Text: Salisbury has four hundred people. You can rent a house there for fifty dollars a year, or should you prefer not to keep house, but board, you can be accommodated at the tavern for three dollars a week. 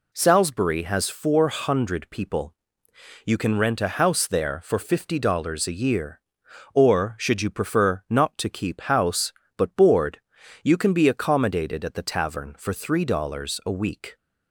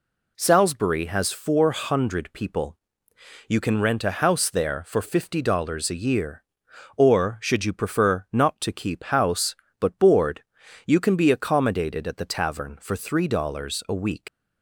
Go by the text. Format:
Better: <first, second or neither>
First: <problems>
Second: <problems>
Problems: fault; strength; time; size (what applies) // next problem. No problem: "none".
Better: first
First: none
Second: leaves "week" unfinished; at 14.2 s; 105 ms